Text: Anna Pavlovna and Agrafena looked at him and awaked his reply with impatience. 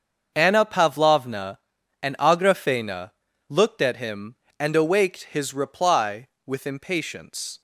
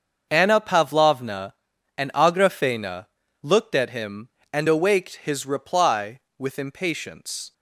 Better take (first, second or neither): neither